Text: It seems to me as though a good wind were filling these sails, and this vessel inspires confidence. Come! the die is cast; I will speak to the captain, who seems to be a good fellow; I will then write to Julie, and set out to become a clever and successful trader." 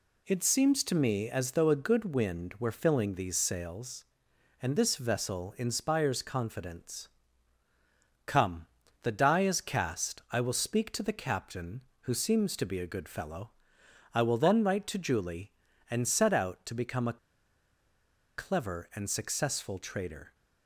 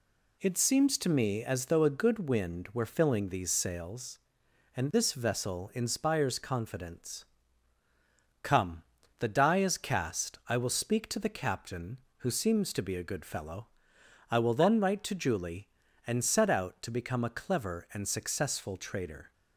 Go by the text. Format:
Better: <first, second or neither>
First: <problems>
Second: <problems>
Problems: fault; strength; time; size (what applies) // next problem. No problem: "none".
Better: second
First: pauses between "a" and "clever"; at 17.1 s; 1.1 s long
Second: none